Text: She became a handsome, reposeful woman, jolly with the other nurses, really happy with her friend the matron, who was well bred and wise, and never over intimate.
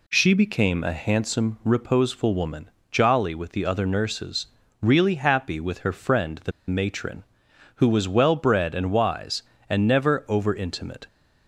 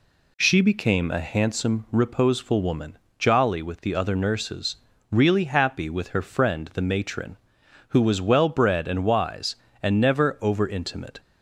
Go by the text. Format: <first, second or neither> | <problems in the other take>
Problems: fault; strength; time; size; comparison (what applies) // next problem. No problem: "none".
second | pauses between "the" and "matron"; slight; at 6.5 s; 0.17 s long